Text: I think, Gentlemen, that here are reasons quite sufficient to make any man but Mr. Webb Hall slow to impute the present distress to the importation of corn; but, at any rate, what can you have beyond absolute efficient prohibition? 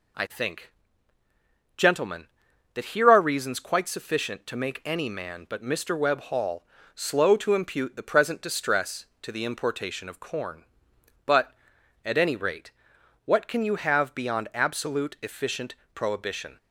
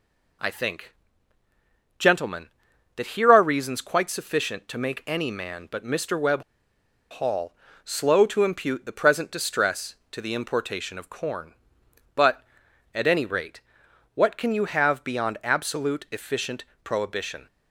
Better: first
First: pauses between "Hall" and "slow"; slight; at 6.6 s; 0.30 s long // pauses between "efficient" and "prohibition"; slight; at 15.7 s; 0.18 s long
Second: pauses between "Webb" and "Hall"; noticeable; at 6.4 s; 0.67 s long // pauses between "Hall" and "slow"; slight; at 7.5 s; 0.30 s long // pauses between "efficient" and "prohibition"; slight; at 16.6 s; 0.18 s long

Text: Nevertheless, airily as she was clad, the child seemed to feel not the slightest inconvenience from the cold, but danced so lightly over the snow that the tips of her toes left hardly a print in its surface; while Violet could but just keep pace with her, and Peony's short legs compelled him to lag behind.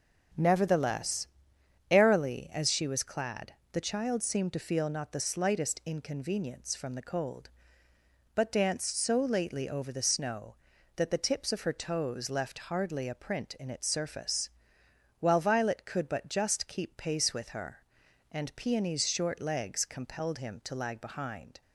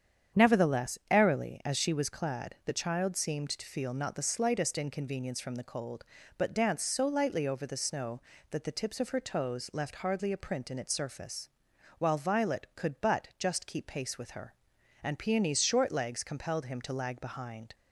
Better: second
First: starts louder than the rest; until 2.0 s; 7 dB // says "lately" for "lightly"; at 9.2 s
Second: starts louder than the rest; strong; until 1.4 s; 8 dB

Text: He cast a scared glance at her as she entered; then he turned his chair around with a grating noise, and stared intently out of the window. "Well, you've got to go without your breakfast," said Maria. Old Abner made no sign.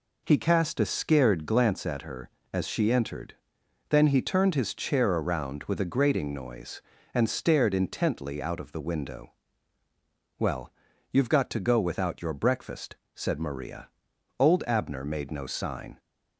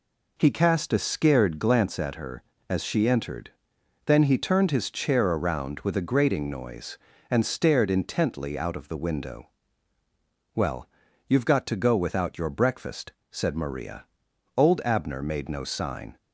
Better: neither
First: none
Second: none

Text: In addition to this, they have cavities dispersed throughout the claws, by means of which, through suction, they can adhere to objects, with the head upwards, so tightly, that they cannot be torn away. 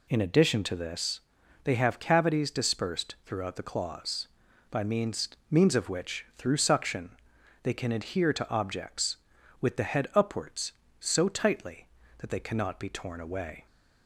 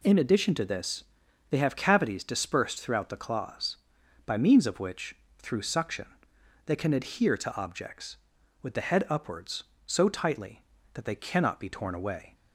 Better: second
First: says "means" twice; at 5.4 s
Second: none

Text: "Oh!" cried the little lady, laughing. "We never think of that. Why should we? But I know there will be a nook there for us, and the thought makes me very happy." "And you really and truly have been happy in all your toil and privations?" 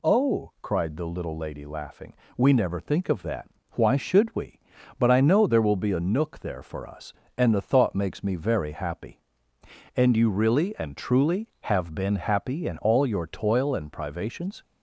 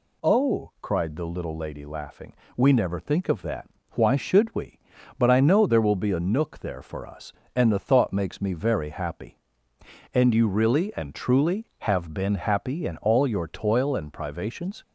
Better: neither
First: none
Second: none

